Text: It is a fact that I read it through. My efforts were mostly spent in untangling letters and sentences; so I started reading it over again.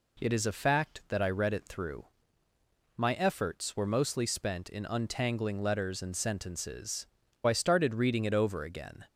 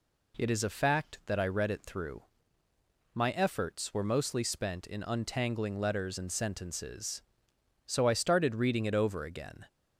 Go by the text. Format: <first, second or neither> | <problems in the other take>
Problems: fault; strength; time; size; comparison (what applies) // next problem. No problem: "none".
second | skips "so"; at 7.2 s